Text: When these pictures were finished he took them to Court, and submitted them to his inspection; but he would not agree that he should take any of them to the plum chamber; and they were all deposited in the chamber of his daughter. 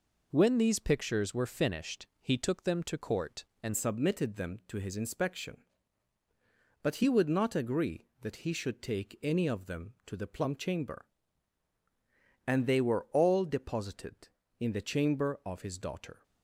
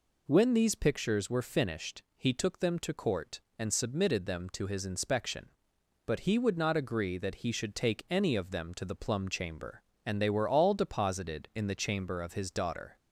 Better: second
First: changes voice at "submitted"; from 3.7 s on; 12.5 s long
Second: none

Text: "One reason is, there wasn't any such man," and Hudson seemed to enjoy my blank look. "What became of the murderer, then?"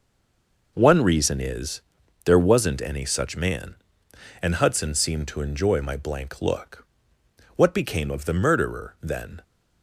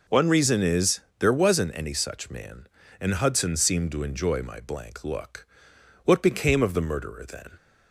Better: second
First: stays silent before the first word; slight; until 0.7 s; 0.7 s long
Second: none

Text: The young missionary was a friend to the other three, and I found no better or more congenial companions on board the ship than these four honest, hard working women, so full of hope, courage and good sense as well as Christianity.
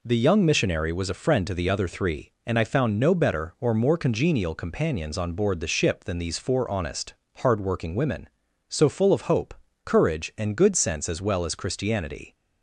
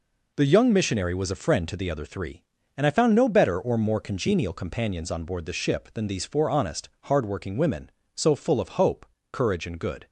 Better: first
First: none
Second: stops before "sense as well as Christianity"; at 10.0 s

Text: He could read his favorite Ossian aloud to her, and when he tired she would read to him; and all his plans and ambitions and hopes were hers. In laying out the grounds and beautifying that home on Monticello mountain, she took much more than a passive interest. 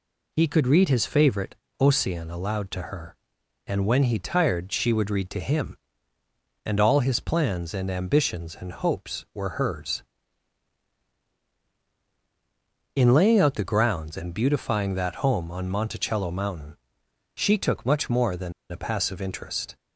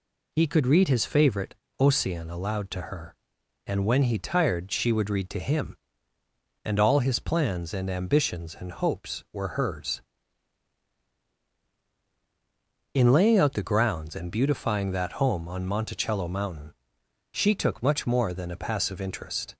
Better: second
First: pauses between "favorite" and "Ossian"; slight; at 1.5 s; 0.22 s long // pauses between "than" and "a"; slight; at 18.5 s; 0.18 s long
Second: pauses between "favorite" and "Ossian"; slight; at 1.5 s; 0.22 s long

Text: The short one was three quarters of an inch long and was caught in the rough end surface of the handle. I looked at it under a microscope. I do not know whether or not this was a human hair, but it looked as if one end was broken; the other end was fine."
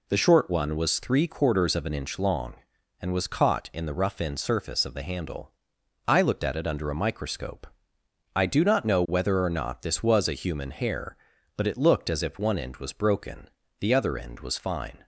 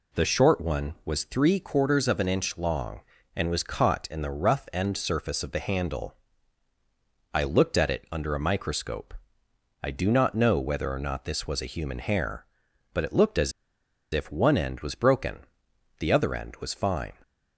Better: first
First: none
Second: pauses between "as" and "if"; noticeable; at 13.5 s; 0.62 s long

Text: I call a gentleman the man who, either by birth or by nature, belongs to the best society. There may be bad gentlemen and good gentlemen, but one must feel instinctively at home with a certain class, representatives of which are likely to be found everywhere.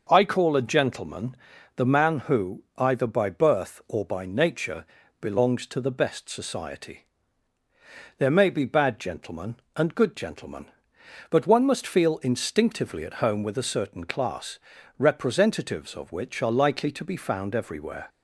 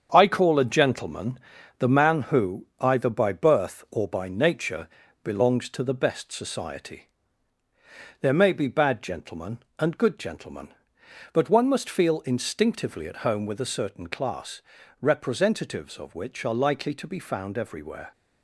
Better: first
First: pauses between "gentleman" and "the"; at 1.3 s; 0.40 s long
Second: gets quieter; throughout; 6.5 dB // pauses between "gentleman" and "the"; at 1.3 s; 0.40 s long

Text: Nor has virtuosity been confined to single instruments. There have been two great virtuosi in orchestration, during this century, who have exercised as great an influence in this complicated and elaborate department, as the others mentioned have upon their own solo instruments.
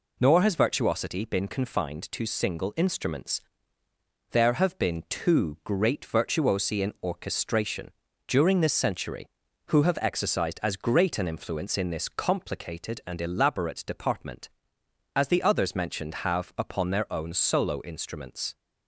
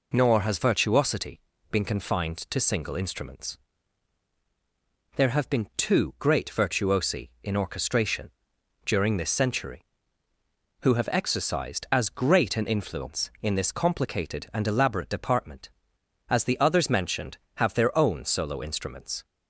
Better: first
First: none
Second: pauses between "virtuosity" and "been"; slight; at 1.4 s; 0.30 s long // skips "upon"; at 17.7 s

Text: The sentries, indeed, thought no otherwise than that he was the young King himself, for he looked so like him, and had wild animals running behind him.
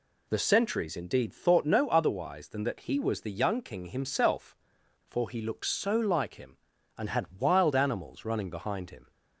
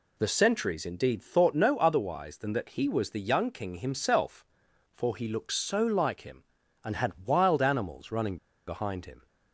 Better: first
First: none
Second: pauses between "running" and "behind"; slight; at 8.3 s; 0.31 s long

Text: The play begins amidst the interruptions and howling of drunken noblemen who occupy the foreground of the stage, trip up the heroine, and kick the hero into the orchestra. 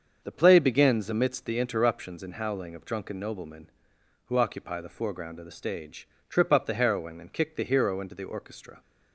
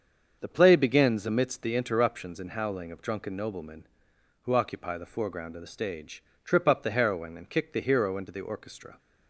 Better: neither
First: starts louder than the rest; until 1.2 s; 7 dB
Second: starts louder than the rest; until 1.4 s; 7 dB

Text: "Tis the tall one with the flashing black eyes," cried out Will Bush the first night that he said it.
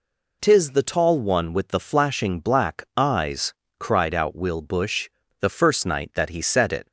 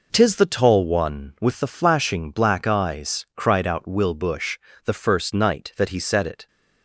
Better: neither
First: pauses between "Bush" and "the"; slight; at 5.0 s; 0.32 s long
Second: pauses between "Bush" and "the"; slight; at 4.5 s; 0.24 s long

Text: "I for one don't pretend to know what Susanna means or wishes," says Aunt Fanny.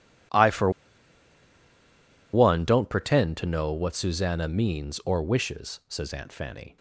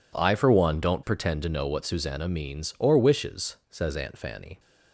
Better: second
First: pauses between "for" and "one"; strong; at 0.6 s; 1.6 s long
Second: none

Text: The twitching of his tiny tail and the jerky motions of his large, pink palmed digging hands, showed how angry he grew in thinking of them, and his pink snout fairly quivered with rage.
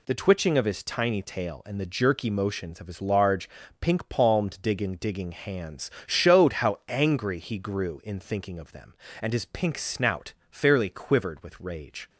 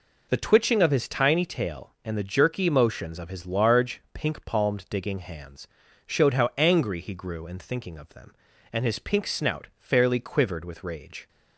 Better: second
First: says "digging" twice; at 4.9 s // pauses between "snout" and "fairly"; slight; at 10.3 s; 0.16 s long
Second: none

